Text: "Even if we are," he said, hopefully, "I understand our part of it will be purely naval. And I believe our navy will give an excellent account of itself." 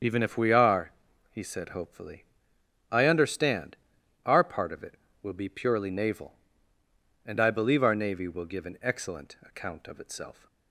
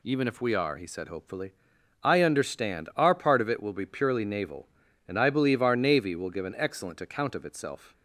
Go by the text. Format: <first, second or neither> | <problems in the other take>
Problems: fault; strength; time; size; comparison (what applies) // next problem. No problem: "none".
second | loses the start of "Even"; at 0.0 s; 55 ms // starts louder than the rest; until 1.4 s; 7 dB // pauses between "understand" and "our"; noticeable; at 3.7 s; 0.50 s long